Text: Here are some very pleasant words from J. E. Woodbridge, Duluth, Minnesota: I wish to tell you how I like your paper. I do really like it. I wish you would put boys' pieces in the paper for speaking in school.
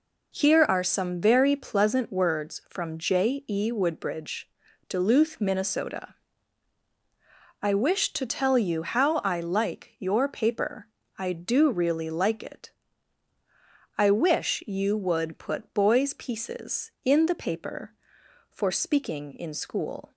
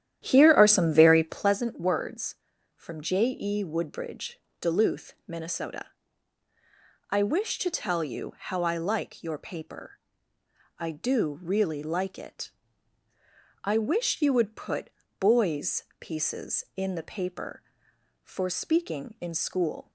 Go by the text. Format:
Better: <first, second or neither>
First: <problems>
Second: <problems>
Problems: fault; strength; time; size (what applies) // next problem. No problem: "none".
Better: first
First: none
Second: starts louder than the rest; strong; until 1.6 s; 11 dB // pauses between "put" and "boys"; slight; at 14.9 s; 0.27 s long // pauses between "boys" and "pieces"; slight; at 15.8 s; 0.16 s long